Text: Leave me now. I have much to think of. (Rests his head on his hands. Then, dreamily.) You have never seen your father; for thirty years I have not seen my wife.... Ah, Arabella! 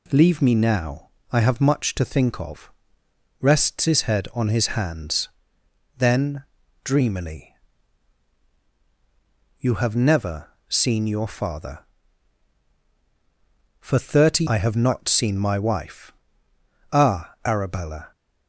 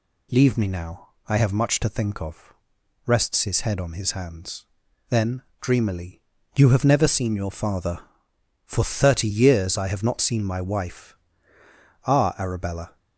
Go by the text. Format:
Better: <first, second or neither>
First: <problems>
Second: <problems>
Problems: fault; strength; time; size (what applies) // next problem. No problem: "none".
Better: second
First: pauses between "never" and "seen"; slight; at 10.4 s; 0.20 s long // skips "years"; at 14.4 s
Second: none